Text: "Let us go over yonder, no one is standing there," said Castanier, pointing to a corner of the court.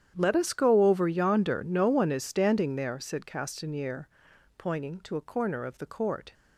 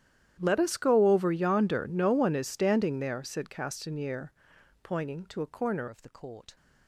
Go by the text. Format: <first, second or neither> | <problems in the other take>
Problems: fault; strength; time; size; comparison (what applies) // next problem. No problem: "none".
first | starts louder than the rest; strong; until 1.4 s; 11 dB; strong in the first // changes voice at "of"; from 5.8 s on; 0.7 s long